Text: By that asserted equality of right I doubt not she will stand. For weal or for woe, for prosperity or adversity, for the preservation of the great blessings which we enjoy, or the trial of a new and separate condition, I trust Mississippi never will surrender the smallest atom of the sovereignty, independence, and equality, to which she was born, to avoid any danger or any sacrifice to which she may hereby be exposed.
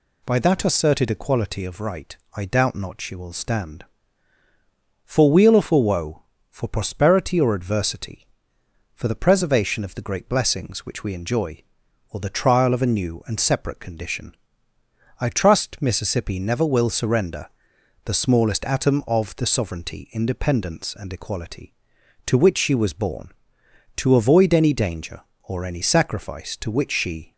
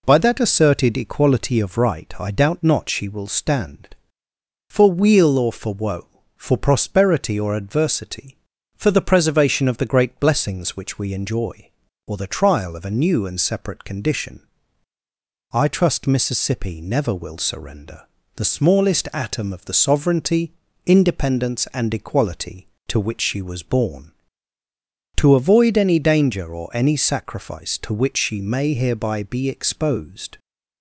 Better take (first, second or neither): second